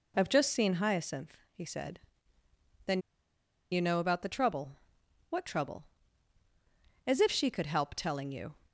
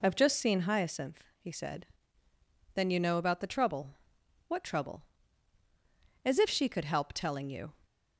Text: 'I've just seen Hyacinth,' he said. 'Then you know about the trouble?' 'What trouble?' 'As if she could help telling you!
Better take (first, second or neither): second